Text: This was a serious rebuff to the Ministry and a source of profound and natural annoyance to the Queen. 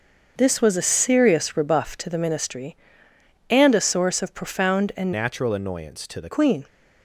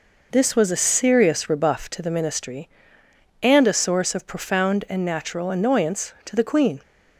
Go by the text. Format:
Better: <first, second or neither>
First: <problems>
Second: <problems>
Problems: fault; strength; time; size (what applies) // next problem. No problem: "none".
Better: second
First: starts louder than the rest; until 1.3 s; 6.5 dB // changes voice from "natural" to "the"; from 5.1 to 6.2 s; 1.1 s long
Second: none